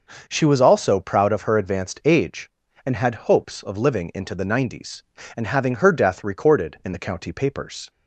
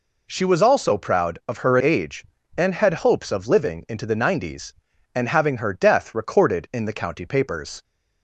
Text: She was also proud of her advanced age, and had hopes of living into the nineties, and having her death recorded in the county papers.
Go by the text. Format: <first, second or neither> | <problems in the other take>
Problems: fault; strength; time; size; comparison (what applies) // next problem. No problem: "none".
first | skips "advanced"; at 1.7 s